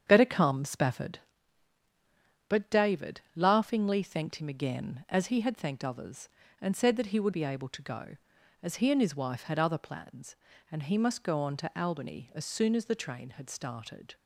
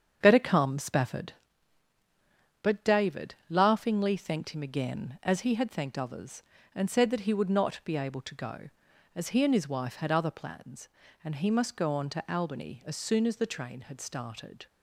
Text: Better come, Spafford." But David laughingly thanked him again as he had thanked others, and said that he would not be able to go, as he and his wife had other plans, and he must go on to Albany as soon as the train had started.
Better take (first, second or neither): second